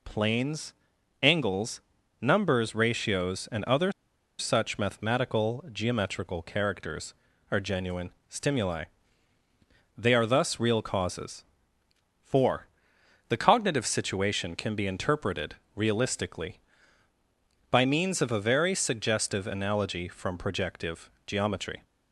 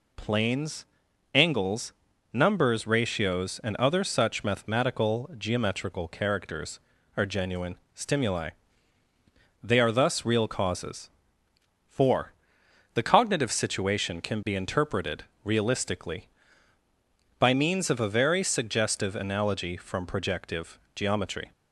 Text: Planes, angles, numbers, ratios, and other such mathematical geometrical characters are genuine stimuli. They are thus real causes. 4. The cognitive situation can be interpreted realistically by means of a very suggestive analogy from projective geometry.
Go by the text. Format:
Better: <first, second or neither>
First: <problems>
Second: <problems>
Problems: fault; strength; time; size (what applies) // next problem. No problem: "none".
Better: second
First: pauses between "other" and "such"; noticeable; at 3.9 s; 0.48 s long // pauses between "genuine" and "stimuli"; slight; at 8.1 s; 0.18 s long // pauses between "interpreted" and "realistically"; slight; at 15.5 s; 0.20 s long // pauses between "projective" and "geometry"; slight; at 21.0 s; 0.16 s long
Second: pauses between "genuine" and "stimuli"; slight; at 7.7 s; 0.18 s long // pauses between "interpreted" and "realistically"; slight; at 15.2 s; 0.20 s long // pauses between "projective" and "geometry"; slight; at 20.7 s; 0.16 s long